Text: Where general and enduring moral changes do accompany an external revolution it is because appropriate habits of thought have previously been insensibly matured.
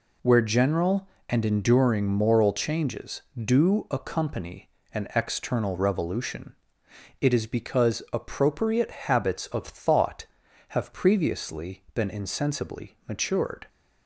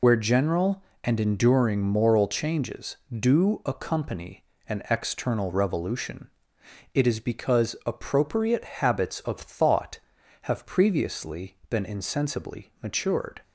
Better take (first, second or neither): first